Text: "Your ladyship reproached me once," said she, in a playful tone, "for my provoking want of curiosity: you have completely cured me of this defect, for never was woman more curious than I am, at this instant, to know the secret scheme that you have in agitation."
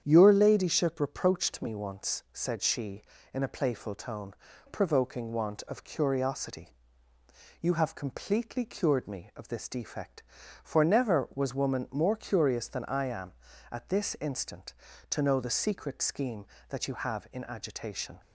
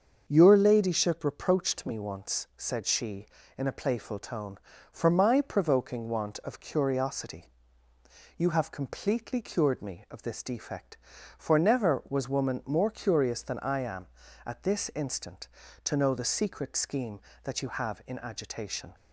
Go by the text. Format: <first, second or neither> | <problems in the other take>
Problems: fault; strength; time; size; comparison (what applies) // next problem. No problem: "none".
second | starts louder than the rest; strong; until 1.0 s; 8.5 dB; also in the second // skips "for my"; at 4.5 s